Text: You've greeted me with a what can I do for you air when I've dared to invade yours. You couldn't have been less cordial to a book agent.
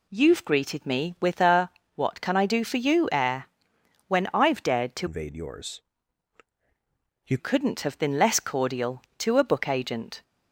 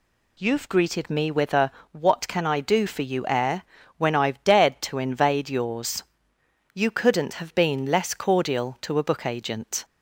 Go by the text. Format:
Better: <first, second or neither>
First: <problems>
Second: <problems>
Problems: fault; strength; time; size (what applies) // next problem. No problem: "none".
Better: second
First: pauses between "a" and "what"; slight; at 1.6 s; 0.24 s long // pauses between "air" and "when"; noticeable; at 3.4 s; 0.62 s long // changes voice from "invade" to "You"; from 5.0 to 7.3 s; 2.3 s long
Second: pauses between "a" and "what"; slight; at 1.7 s; 0.22 s long // pauses between "air" and "when"; slight; at 3.6 s; 0.34 s long